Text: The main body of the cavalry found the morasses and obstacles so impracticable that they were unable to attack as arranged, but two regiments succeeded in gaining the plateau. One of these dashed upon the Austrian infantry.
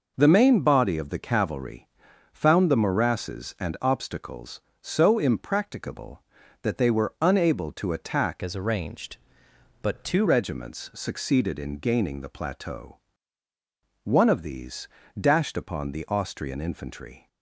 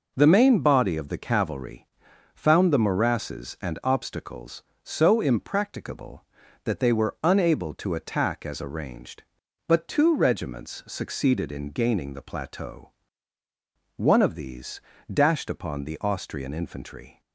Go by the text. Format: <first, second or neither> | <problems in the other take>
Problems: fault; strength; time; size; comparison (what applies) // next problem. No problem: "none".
second | pauses between "cavalry" and "found"; at 1.8 s; 0.44 s long; noticeable in the second // changes voice from "as" to "two"; from 8.4 to 10.2 s; 1.8 s long // pauses between "these" and "dashed"; slight; at 14.8 s; 0.32 s long; slight in the second